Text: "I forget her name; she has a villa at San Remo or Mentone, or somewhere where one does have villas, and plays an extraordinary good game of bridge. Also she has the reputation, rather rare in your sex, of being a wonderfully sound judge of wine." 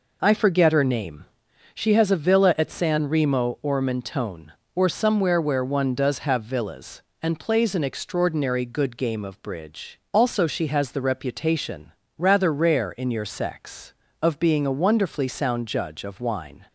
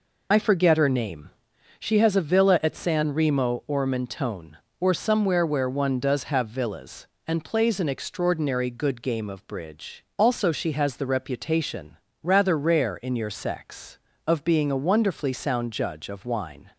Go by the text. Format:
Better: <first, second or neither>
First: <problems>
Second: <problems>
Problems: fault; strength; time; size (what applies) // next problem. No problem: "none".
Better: first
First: none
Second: loses the start of "I"; at 0.3 s; 35 ms